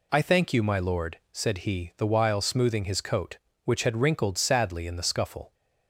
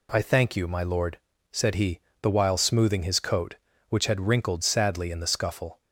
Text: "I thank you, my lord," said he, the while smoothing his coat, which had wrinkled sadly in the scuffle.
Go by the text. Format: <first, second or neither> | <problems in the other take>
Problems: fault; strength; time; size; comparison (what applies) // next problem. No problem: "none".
neither | none